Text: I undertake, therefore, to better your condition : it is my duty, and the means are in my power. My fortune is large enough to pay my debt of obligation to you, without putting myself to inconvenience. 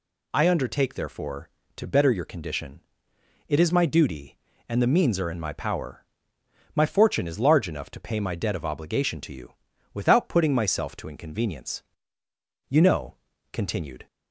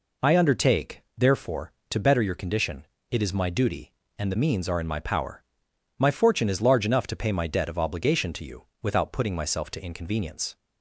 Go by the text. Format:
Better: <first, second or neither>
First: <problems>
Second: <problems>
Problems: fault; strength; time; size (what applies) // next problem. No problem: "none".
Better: second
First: goes on to say "You know continued"; from 12.6 s on; 1.3 s long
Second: none